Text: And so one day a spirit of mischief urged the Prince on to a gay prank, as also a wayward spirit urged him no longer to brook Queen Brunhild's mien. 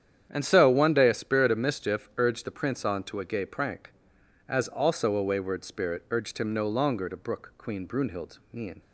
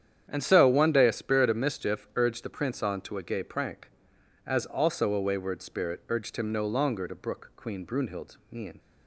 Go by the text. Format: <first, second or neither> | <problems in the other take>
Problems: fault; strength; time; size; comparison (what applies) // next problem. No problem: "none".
neither | starts louder than the rest; strong; the same in both